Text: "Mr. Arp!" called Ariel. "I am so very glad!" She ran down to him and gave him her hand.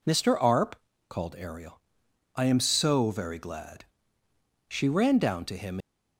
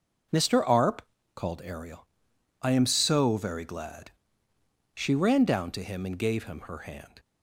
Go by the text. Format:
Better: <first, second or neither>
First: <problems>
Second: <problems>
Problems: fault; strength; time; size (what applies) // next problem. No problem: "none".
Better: second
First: stops before "and gave him her hand"; at 5.8 s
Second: none